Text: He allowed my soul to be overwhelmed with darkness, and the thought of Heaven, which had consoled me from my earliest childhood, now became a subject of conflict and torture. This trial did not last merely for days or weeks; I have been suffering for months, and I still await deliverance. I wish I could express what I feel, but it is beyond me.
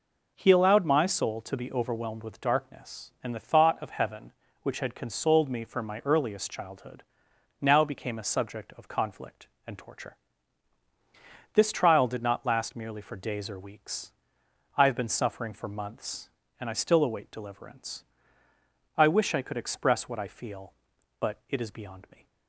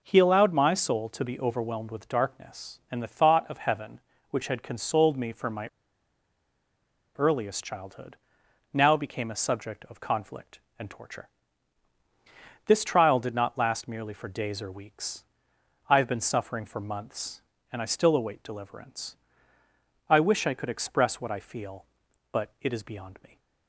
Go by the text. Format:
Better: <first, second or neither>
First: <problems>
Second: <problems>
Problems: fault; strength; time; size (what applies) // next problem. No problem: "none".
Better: first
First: none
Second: pauses between "my" and "earliest"; strong; at 5.6 s; 1.4 s long